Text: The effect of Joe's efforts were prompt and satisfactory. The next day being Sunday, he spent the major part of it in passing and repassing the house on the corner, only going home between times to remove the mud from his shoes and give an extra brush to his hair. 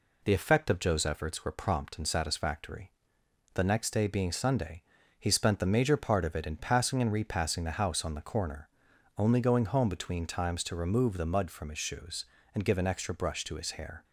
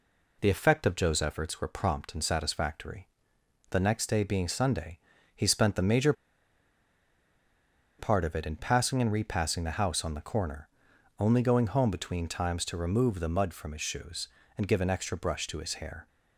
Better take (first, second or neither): first